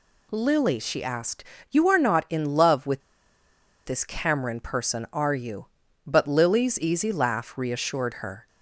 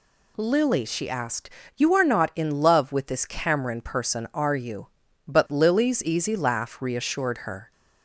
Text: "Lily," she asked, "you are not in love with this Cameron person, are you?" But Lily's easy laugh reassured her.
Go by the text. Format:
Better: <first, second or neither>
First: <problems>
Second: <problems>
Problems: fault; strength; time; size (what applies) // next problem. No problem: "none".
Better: second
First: pauses between "with" and "this"; noticeable; at 3.0 s; 0.84 s long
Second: none